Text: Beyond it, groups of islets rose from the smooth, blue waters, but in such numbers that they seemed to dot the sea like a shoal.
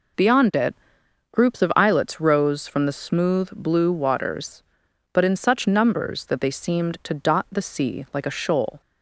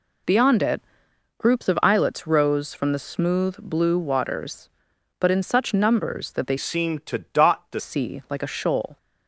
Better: first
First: none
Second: changes voice from "seemed" to "the"; from 6.5 to 7.8 s; 1.3 s long

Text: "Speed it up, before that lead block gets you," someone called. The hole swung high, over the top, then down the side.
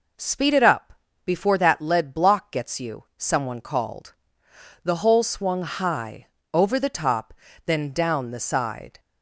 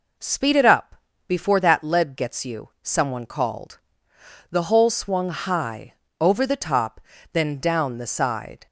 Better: first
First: none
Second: skips "block"; at 2.1 s

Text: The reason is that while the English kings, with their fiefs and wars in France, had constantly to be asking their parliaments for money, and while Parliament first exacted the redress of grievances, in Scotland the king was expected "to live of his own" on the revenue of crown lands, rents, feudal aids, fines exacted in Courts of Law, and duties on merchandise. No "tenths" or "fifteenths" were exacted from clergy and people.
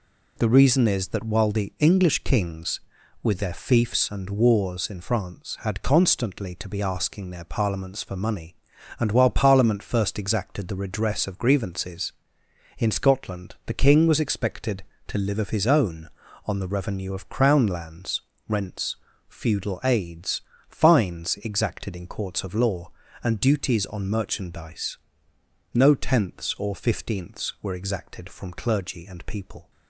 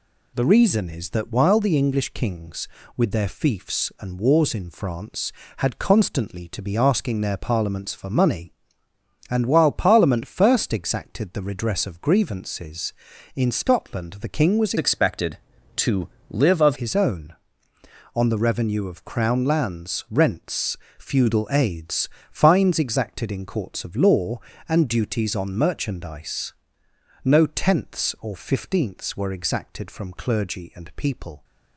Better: first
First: none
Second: changes voice from "expected" to "of"; from 14.7 to 16.7 s; 2.0 s long // pauses between "to" and "live"; slight; at 16.0 s; 0.20 s long

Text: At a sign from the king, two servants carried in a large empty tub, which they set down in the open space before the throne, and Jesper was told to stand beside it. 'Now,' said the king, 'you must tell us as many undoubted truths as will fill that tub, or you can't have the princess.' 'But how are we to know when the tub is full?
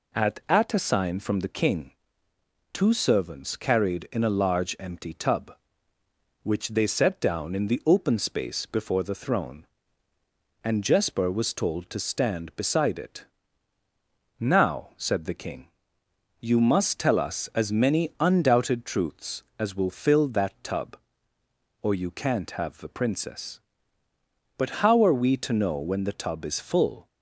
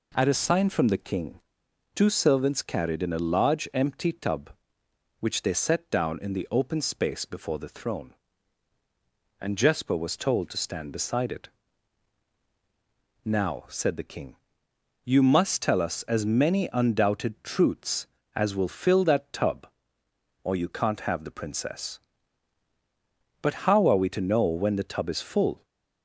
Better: second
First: says "At" twice; at 0.4 s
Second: none

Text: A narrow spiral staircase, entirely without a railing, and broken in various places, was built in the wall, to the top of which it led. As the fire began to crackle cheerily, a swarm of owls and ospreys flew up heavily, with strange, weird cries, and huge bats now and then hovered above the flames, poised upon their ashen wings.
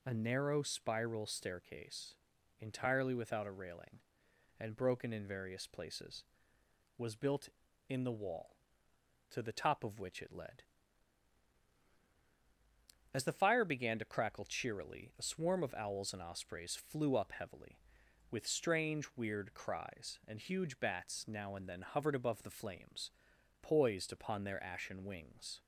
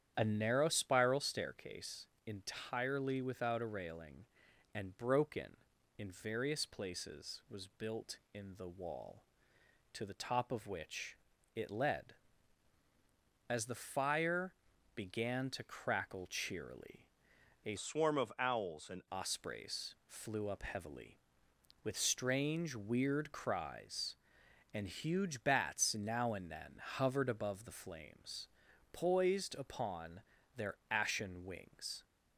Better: first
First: none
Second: starts louder than the rest; strong; until 1.1 s; 9.5 dB // pauses between "which" and "it"; slight; at 11.1 s; 0.36 s long // pauses between "fire" and "began"; at 14.5 s; 0.42 s long // changes voice from "swarm" to "and"; from 17.7 to 19.0 s; 1.3 s long // pauses between "upon" and "their"; slight; at 30.2 s; 0.34 s long

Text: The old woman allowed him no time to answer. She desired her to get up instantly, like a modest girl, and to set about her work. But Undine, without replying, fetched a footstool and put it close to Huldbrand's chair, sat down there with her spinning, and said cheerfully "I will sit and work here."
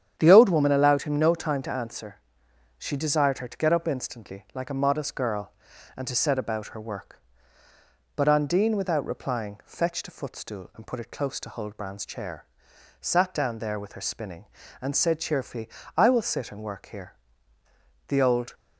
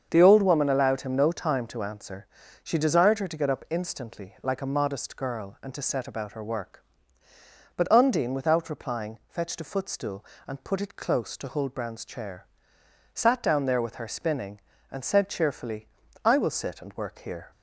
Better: second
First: starts louder than the rest; strong; until 1.1 s; 9 dB // pauses between "cheerfully" and "I"; slight; at 15.6 s; 0.28 s long // goes on to say "The old"; slight; from 18.0 s on; 0.46 s long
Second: starts louder than the rest; strong; until 1.1 s; 7 dB // pauses between "cheerfully" and "I"; at 15.8 s; 0.38 s long

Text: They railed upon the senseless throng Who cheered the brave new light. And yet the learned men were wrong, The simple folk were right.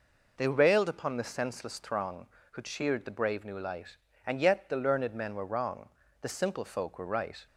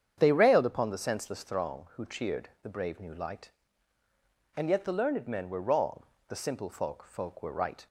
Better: first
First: none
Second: starts louder than the rest; strong; until 1.1 s; 8 dB // says "folk" twice; at 7.0 s

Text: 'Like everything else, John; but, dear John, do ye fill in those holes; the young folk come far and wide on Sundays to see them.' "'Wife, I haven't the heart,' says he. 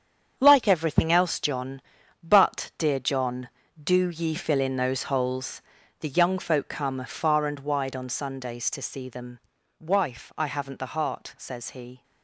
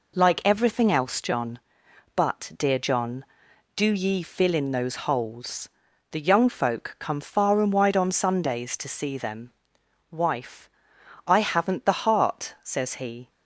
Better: second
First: gets quieter; strong; throughout; 9 dB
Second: none

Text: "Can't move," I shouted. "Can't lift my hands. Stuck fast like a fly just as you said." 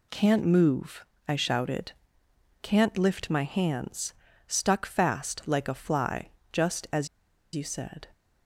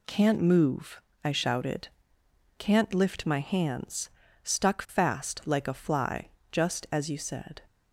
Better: second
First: pauses between "fly" and "just"; slight; at 6.3 s; 0.22 s long // pauses between "as" and "you"; noticeable; at 7.0 s; 0.47 s long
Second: pauses between "fly" and "just"; slight; at 6.2 s; 0.22 s long

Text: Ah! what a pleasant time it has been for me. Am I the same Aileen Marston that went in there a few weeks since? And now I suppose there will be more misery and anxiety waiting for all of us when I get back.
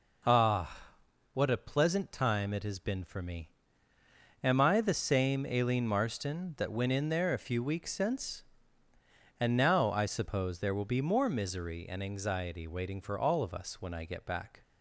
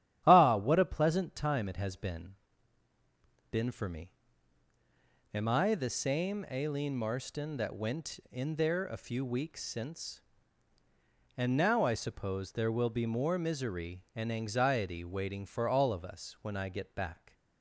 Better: first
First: none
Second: starts louder than the rest; strong; until 1.2 s; 11 dB // says "been" twice; at 3.5 s

